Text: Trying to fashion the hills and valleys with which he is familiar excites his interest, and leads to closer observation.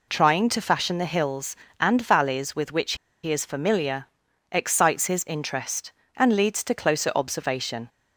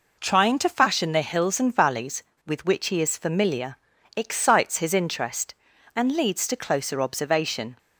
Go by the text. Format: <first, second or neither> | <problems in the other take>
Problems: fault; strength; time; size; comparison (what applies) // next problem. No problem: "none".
second | pauses between "which" and "he"; slight; at 2.9 s; 0.29 s long // pauses between "familiar" and "excites"; at 4.0 s; 0.44 s long; also in the second